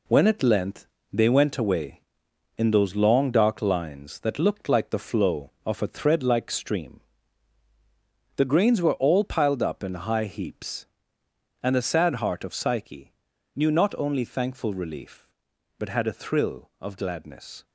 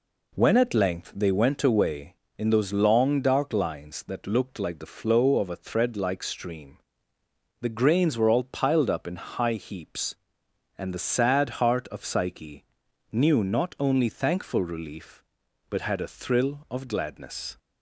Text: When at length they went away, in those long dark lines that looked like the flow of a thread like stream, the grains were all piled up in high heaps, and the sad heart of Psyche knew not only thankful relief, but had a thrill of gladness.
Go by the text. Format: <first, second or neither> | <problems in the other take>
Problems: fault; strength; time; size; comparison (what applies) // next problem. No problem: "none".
second | gets quieter; throughout; 7 dB // pauses between "length" and "they"; slight; at 0.8 s; 0.28 s long // pauses between "Psyche" and "knew"; at 13.1 s; 0.42 s long; noticeable in the second